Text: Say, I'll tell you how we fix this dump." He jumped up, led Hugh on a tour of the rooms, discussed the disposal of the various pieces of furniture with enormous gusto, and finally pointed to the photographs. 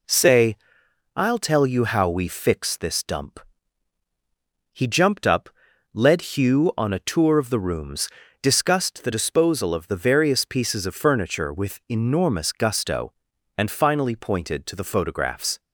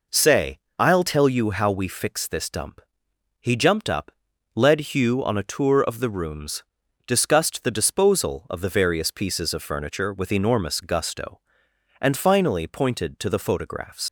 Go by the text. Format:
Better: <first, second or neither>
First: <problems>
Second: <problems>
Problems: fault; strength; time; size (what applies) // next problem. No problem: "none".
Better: first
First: none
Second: leaves "photographs" unfinished; at 14.0 s; 110 ms